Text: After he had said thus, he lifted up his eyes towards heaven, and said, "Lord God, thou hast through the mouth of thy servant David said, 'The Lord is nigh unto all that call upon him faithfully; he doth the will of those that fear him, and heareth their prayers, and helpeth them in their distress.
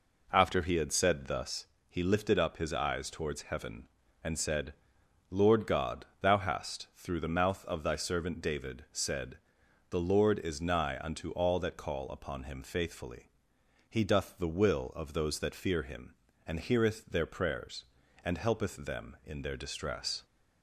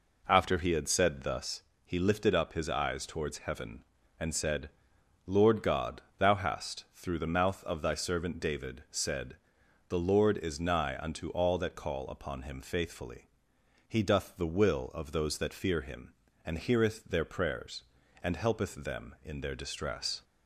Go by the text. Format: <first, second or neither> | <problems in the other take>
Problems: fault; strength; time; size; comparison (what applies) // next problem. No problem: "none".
neither | none